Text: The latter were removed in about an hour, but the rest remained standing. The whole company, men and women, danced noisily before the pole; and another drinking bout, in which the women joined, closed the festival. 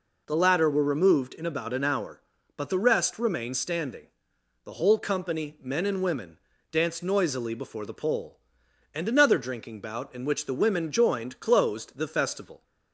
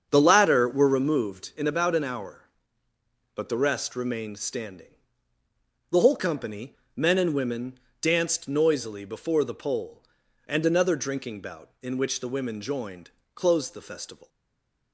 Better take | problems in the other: first | starts louder than the rest; strong; until 1.1 s; 7 dB // stays silent after the last word; slight; from 14.2 s on; 0.7 s long

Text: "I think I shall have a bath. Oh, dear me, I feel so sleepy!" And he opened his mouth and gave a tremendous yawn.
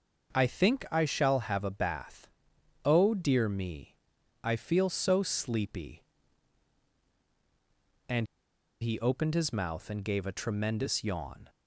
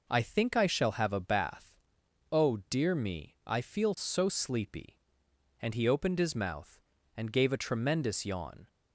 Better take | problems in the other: second | starts louder than the rest; noticeable; until 1.3 s; 6 dB // pauses between "And" and "he"; noticeable; at 8.2 s; 0.56 s long

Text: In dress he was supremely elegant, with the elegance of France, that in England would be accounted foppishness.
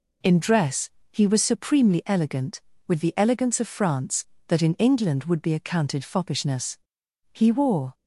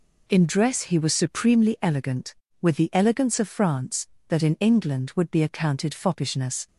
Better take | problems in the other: second | pauses between "dress" and "he"; slight; at 0.9 s; 0.22 s long // goes on to say "He wore"; noticeable; from 7.3 s on; 0.62 s long

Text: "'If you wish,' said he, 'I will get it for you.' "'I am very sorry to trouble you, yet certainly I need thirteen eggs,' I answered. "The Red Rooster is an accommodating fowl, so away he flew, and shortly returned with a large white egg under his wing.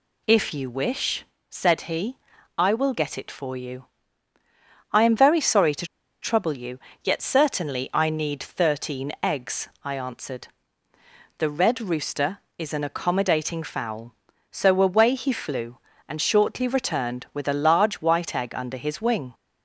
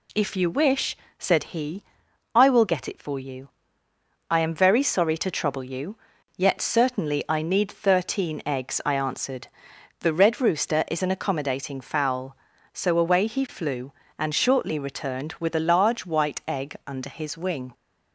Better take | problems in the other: second | pauses between "to" and "trouble"; at 5.8 s; 0.36 s long

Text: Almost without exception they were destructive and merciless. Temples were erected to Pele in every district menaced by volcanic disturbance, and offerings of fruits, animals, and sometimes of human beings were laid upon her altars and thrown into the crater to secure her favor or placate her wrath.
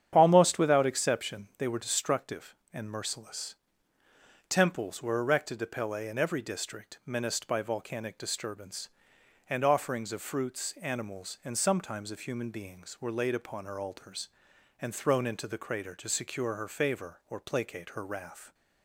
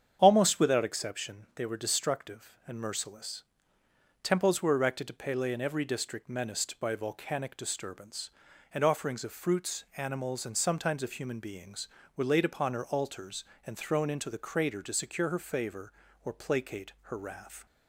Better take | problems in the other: neither | starts louder than the rest; strong; the same in both

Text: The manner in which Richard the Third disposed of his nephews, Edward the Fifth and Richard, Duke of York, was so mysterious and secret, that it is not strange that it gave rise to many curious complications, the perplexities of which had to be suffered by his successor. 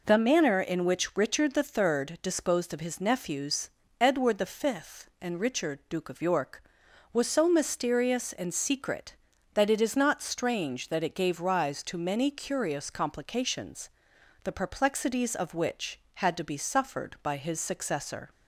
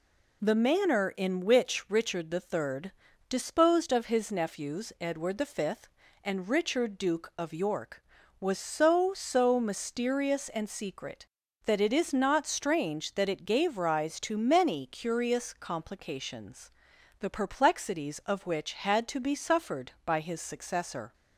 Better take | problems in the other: first | pauses between "Third" and "disposed"; slight; at 2.9 s; 0.36 s long // says "so" twice; at 9.1 s

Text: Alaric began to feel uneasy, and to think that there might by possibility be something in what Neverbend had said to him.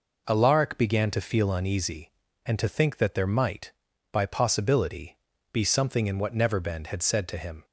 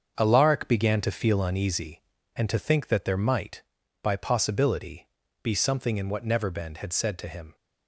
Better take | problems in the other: first | gets quieter; strong; throughout; 9.5 dB // pauses between "possibility" and "be"; slight; at 5.0 s; 0.34 s long; slight in the first

